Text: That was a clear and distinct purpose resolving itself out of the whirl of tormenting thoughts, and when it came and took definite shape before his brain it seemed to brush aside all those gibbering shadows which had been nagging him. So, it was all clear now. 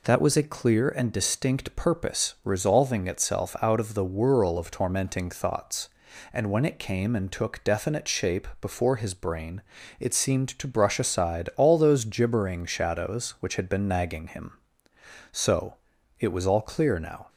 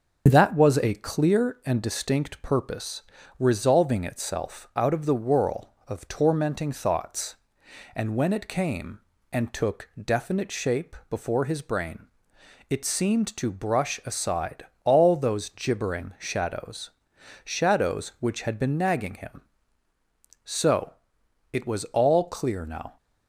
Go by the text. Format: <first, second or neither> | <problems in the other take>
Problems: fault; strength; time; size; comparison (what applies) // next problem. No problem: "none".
first | starts louder than the rest; until 1.2 s; 6 dB // pauses between "purpose" and "resolving"; slight; at 3.0 s; 0.36 s long // pauses between "brain" and "it"; noticeable; at 12.0 s; 0.60 s long; slight in the first // pauses between "aside" and "all"; slight; at 14.6 s; 0.18 s long // says "shadows" twice; at 17.4 s